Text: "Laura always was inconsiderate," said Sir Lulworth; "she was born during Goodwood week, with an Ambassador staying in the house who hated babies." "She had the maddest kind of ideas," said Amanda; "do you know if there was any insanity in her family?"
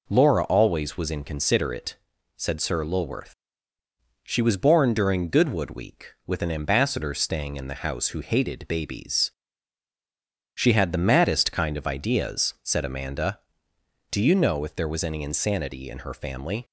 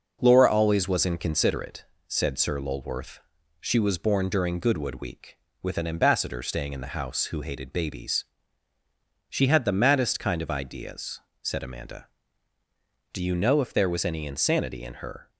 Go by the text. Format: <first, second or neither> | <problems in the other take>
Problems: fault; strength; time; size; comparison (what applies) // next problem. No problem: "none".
first | stops before "family"; at 15.2 s